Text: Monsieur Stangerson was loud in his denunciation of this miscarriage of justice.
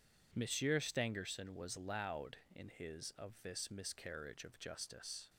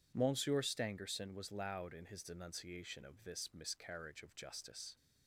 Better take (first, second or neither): second